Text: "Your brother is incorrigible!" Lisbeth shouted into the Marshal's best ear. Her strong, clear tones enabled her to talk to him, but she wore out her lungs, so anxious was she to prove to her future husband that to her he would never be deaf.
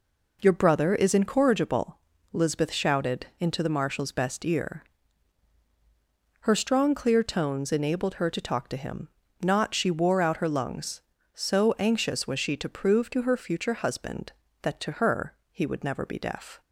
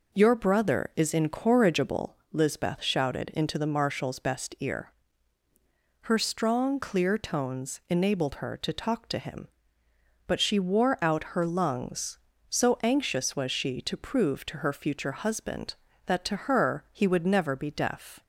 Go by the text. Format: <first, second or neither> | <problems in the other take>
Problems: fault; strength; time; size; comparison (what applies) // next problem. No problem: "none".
second | says "not" for "but"; at 9.4 s // pauses between "her" and "he"; slight; at 15.3 s; 0.16 s long